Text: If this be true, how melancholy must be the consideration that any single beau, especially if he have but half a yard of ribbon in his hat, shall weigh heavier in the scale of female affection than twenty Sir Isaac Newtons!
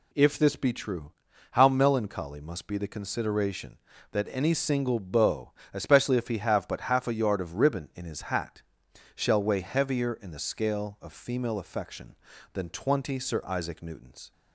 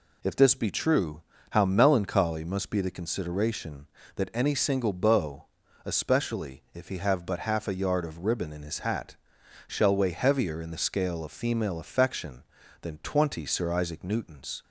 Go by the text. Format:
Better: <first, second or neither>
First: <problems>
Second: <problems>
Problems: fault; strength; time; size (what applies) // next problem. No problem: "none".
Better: neither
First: none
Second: none